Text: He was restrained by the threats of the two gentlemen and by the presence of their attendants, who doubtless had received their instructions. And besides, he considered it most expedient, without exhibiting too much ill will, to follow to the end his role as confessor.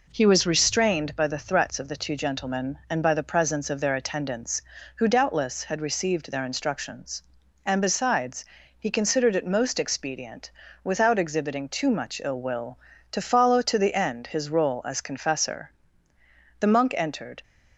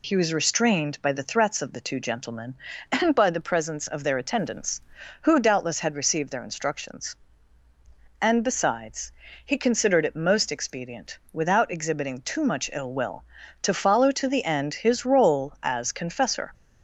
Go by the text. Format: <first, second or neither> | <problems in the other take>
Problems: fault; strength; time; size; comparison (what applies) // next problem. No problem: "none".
second | goes on to say "The monk entered"; noticeable; from 16.6 s on; 0.82 s long